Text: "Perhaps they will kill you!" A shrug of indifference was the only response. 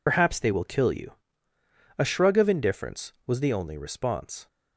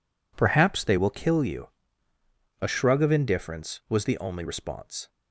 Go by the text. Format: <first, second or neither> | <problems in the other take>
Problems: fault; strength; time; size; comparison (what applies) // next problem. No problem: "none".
second | loses the start of "Perhaps"; at 0.0 s; 95 ms